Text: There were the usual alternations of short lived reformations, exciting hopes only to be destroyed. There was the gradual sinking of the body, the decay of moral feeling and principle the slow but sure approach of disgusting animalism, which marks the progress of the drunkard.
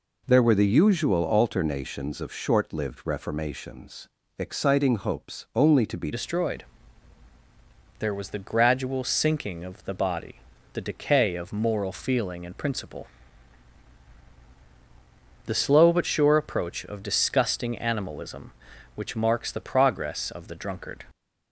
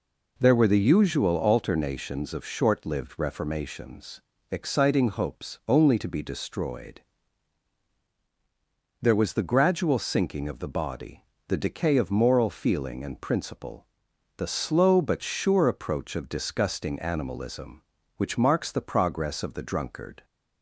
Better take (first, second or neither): second